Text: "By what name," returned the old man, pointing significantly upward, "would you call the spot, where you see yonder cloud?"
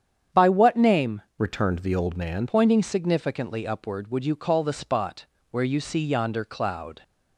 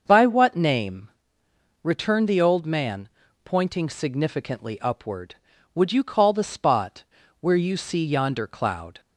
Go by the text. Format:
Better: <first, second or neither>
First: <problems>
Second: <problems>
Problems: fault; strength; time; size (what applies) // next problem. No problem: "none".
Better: second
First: starts louder than the rest; strong; until 1.5 s; 8.5 dB // changes voice from "returned" to "man"; from 1.3 to 2.4 s; 1.1 s long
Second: starts louder than the rest; until 1.0 s; 6.5 dB